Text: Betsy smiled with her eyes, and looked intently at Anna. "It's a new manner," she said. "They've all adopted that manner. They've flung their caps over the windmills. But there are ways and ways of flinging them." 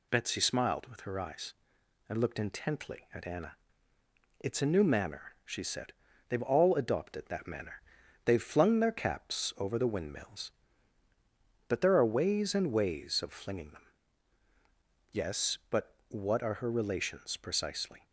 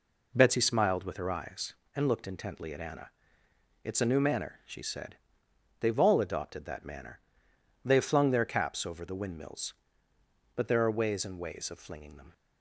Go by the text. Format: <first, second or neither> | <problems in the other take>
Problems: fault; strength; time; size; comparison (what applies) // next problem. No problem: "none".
second | goes on to say "Yes but what are her relations precisely"; strong; from 15.1 s on; 2.9 s long